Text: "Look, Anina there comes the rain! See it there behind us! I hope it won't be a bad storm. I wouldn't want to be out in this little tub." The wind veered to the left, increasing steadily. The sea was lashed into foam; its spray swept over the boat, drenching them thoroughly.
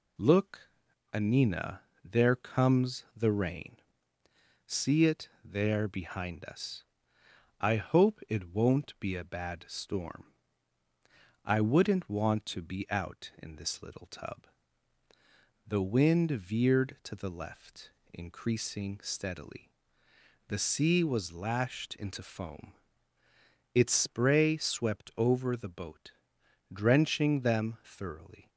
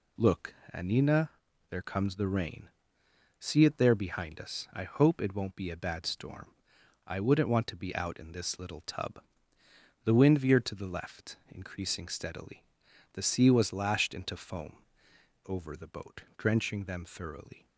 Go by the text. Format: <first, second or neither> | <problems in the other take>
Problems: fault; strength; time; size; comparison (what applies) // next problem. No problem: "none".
first | pauses between "Anina" and "there"; at 1.2 s; 0.40 s long; slight in the first // skips "its spray swept"; at 15.1 s